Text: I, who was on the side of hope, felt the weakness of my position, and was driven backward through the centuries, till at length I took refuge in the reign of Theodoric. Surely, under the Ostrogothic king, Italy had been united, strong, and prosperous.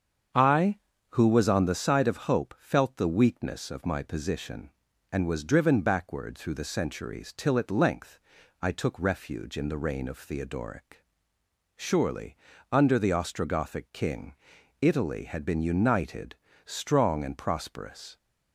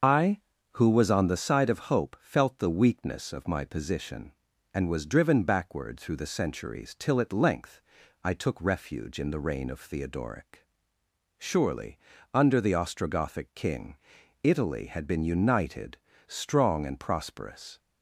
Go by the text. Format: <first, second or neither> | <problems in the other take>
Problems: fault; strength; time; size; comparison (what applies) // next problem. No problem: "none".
first | loses the start of "I"; at 0.0 s; 65 ms // starts louder than the rest; until 1.3 s; 6.5 dB; strong in the first // pauses between "length" and "I"; at 7.8 s; 0.42 s long; also in the first